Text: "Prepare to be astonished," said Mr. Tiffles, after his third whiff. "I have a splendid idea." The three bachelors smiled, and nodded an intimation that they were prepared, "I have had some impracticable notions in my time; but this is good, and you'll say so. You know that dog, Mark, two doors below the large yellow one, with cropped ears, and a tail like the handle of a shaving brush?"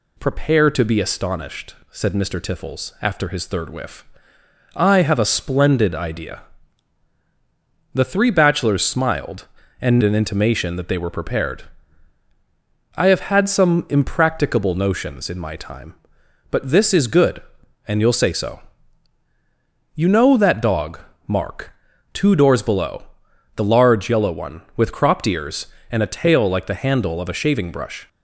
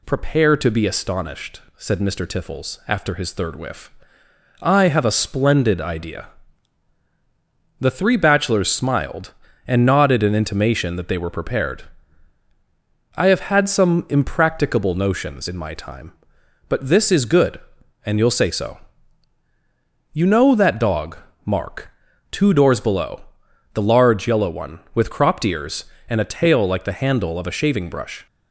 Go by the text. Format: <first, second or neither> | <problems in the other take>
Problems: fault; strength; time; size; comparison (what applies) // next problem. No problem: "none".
second | skips "nodded"; at 10.0 s // pauses between "below" and "the"; noticeable; at 23.0 s; 0.54 s long; noticeable in the second